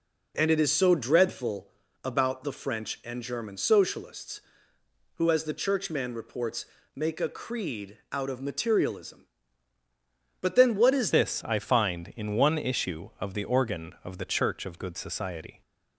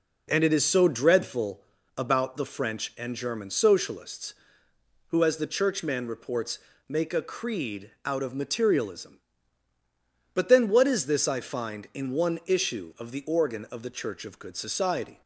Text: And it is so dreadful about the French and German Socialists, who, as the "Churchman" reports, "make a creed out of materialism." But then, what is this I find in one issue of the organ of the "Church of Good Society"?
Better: second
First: pauses between "dreadful" and "about"; slight; at 1.6 s; 0.36 s long // changes voice at "this"; from 11.1 s on; 4.5 s long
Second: pauses between "dreadful" and "about"; slight; at 1.6 s; 0.36 s long

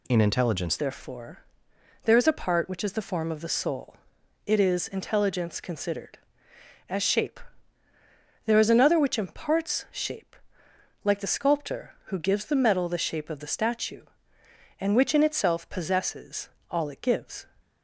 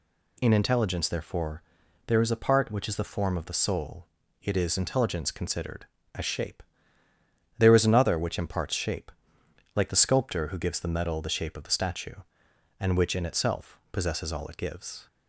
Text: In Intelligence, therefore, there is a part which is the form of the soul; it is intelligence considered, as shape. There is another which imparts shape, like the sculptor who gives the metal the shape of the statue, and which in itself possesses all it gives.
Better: second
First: changes voice at "therefore"; from 0.7 s on; 16.7 s long // pauses between "possesses" and "all"; slight; at 16.5 s; 0.20 s long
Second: none

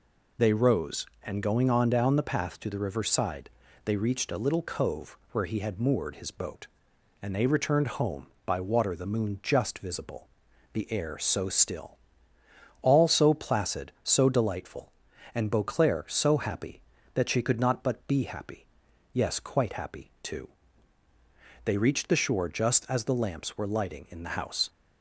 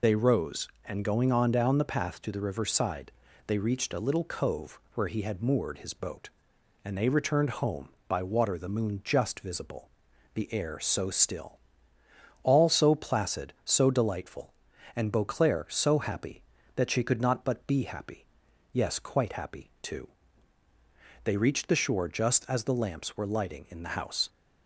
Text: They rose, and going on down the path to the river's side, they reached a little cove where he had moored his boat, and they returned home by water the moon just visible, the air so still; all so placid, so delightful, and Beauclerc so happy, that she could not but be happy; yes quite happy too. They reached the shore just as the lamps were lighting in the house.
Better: first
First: none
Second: loses the start of "They"; at 0.0 s; 35 ms

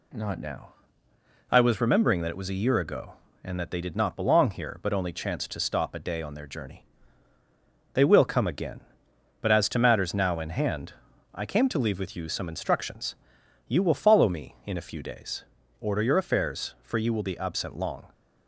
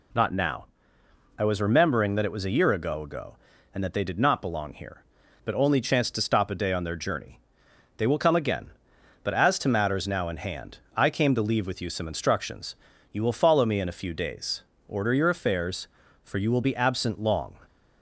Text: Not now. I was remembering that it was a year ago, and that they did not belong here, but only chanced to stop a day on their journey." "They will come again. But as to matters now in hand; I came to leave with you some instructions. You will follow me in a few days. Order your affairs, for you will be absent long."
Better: first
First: none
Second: says "ago" twice; at 3.0 s

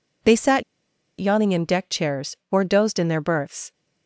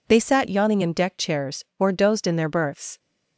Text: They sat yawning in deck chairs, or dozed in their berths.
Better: second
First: pauses between "sat" and "yawning"; noticeable; at 0.6 s; 0.56 s long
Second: none

